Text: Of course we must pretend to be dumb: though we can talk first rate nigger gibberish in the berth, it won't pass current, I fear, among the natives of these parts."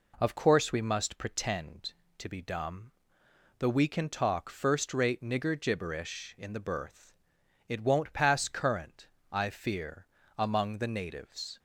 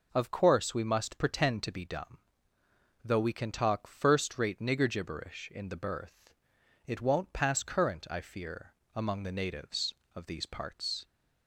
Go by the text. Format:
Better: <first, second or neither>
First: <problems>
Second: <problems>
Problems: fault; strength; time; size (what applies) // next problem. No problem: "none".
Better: second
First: stops before "of these parts"; at 11.5 s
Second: none